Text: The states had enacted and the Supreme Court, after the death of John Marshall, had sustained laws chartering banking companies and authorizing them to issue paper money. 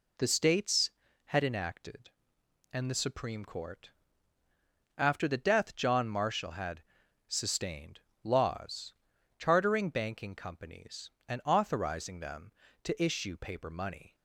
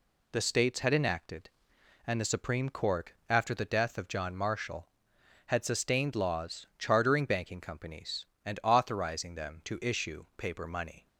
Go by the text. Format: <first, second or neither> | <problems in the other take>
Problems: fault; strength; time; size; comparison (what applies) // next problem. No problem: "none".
second | skips "of"; at 5.7 s // pauses between "had" and "sustained"; at 6.8 s; 0.44 s long // pauses between "sustained" and "laws"; slight; at 8.0 s; 0.22 s long // pauses between "laws" and "chartering"; noticeable; at 8.9 s; 0.46 s long